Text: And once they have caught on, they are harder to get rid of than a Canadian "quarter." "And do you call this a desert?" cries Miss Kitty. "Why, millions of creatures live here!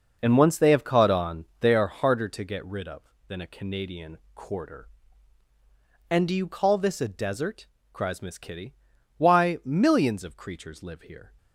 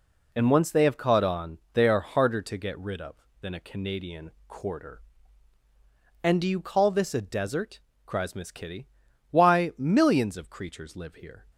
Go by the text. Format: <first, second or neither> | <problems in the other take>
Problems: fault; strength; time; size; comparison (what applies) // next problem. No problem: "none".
second | starts louder than the rest; noticeable; until 1.7 s; 6 dB // pauses between "Canadian" and "quarter"; slight; at 4.1 s; 0.18 s long; slight in the second